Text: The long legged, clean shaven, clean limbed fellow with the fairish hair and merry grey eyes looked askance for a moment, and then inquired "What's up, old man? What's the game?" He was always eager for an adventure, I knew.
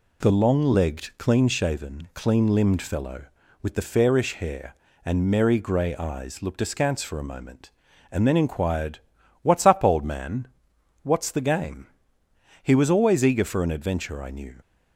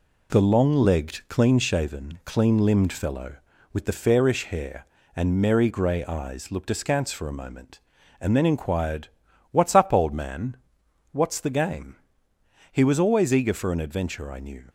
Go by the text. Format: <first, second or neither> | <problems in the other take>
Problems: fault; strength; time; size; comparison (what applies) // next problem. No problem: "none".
first | gets quieter; throughout; 4 dB // pauses between "inquired" and "What's"; at 9.0 s; 0.42 s long; also in the first